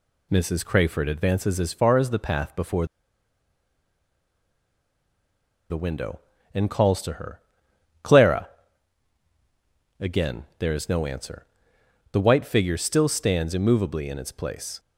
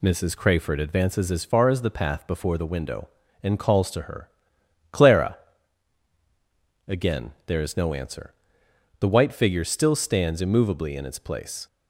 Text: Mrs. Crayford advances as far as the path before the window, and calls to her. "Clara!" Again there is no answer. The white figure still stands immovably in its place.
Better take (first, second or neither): second